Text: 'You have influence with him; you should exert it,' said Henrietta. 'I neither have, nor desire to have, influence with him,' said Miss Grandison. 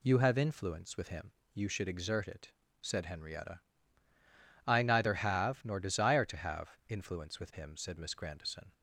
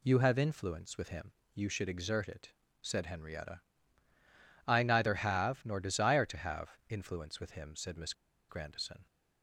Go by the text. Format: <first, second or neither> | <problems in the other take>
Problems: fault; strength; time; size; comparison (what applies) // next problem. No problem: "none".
first | pauses between "Miss" and "Grandison"; at 8.1 s; 0.37 s long